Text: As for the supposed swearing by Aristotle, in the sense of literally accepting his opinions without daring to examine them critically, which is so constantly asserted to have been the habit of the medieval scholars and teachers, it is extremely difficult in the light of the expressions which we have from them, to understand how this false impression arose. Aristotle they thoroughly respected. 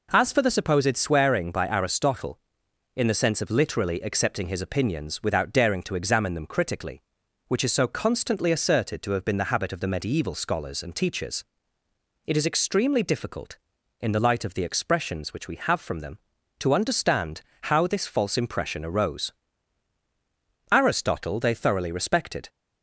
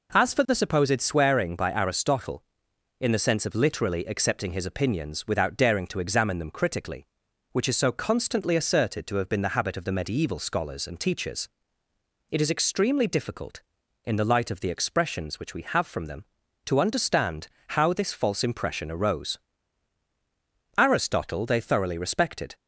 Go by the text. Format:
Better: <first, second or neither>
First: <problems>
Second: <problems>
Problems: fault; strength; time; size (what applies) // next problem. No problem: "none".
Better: neither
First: pauses between "understand" and "how"; slight; at 17.4 s; 0.20 s long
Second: pauses between "understand" and "how"; slight; at 17.4 s; 0.20 s long